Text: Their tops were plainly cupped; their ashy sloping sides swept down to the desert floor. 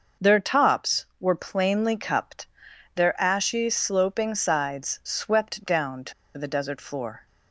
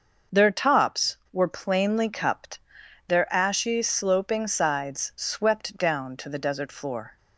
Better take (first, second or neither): second